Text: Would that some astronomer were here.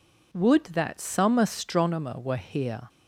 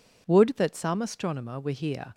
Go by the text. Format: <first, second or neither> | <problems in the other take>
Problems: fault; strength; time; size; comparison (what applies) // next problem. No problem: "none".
neither | none